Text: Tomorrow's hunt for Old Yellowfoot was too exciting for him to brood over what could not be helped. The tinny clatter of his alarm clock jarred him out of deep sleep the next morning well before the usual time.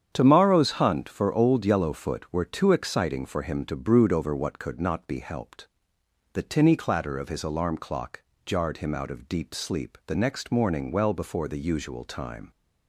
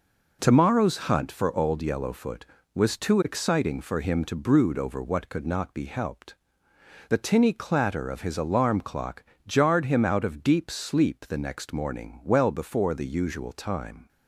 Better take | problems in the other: second | starts louder than the rest; strong; until 1.1 s; 8.5 dB // says "were" for "was"; at 2.3 s // pauses between "clock" and "jarred"; slight; at 8.2 s; 0.22 s long; slight in the second

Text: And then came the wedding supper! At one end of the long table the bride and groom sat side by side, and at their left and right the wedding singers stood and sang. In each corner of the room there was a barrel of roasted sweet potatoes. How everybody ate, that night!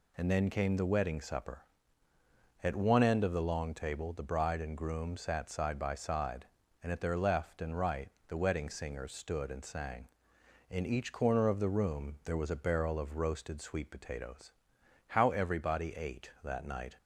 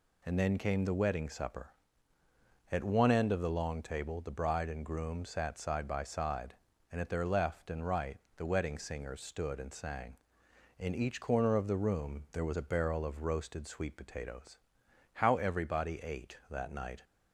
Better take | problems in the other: neither | pauses between "right" and "the"; slight; the same in both

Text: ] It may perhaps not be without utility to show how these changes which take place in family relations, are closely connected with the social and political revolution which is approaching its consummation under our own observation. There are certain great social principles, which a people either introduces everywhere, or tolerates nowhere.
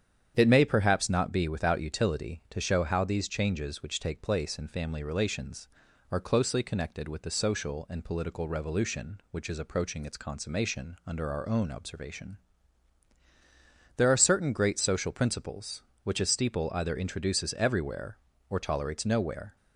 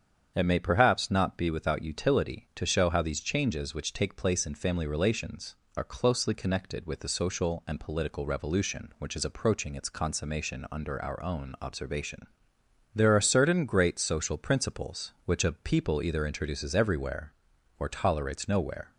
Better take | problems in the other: second | starts louder than the rest; strong; until 1.3 s; 8.5 dB; strong in the second // says "steeple" for "people"; at 16.2 s

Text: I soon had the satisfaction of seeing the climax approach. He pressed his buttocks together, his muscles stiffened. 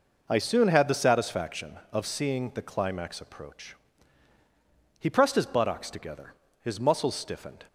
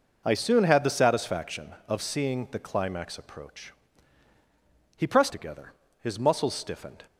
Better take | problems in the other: first | skips "his buttocks"; at 5.2 s

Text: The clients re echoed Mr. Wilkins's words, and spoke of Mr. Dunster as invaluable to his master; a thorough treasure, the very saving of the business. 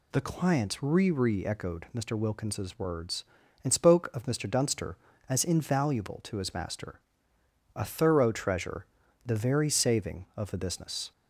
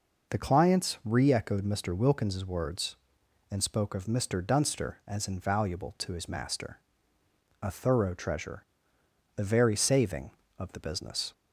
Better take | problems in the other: second | says "re" twice; at 1.0 s

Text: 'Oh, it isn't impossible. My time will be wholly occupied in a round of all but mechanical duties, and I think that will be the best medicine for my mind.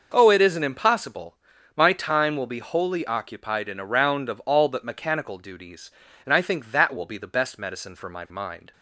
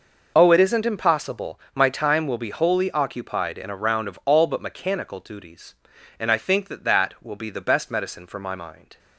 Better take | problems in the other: first | says "that" twice; at 6.8 s

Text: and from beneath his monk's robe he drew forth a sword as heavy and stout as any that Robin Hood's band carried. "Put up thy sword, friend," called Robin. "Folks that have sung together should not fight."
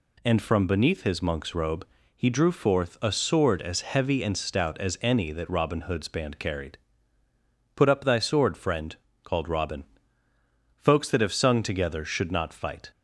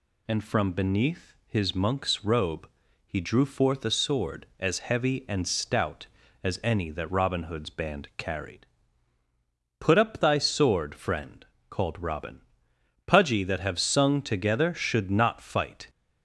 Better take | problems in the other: first | pauses between "robe" and "he"; at 2.6 s; 0.38 s long; slight in the first // says "Pudgy" for "Folks"; at 13.0 s

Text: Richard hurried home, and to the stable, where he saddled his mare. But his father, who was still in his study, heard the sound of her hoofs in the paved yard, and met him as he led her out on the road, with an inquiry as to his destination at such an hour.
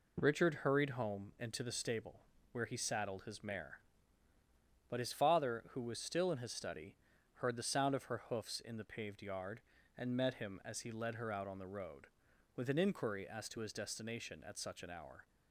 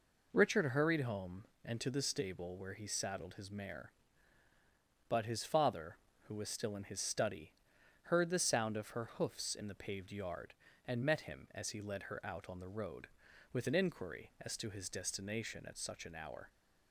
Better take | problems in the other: neither | none

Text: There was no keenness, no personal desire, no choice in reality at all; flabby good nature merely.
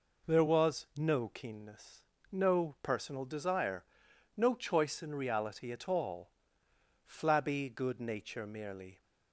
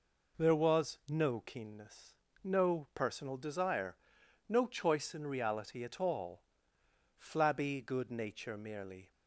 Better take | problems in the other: neither | none

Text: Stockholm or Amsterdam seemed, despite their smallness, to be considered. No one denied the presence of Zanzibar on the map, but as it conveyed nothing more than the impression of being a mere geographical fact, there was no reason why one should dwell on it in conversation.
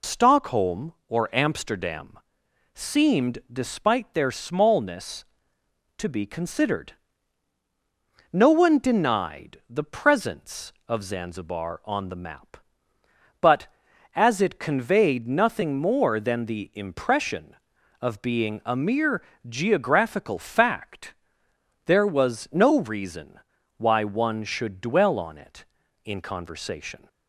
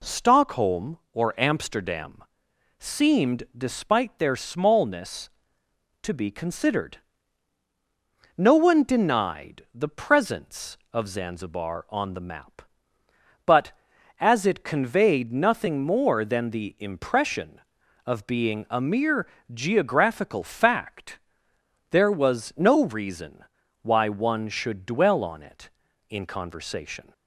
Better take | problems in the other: second | loses the start of "Stockholm"; at 0.0 s; 65 ms // pauses between "Amsterdam" and "seemed"; noticeable; at 2.1 s; 0.58 s long; noticeable in the second // pauses between "mere" and "geographical"; slight; at 19.2 s; 0.24 s long; slight in the second // pauses between "reason" and "why"; at 23.3 s; 0.38 s long; also in the second

